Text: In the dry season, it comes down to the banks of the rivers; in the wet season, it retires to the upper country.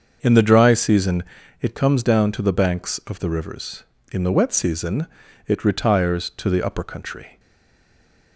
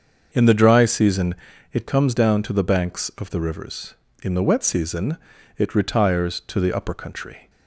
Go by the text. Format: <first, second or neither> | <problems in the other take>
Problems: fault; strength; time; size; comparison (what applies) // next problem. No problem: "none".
second | starts louder than the rest; until 1.2 s; 6.5 dB; also in the second // stays silent after the last word; from 7.3 s on; 1.0 s long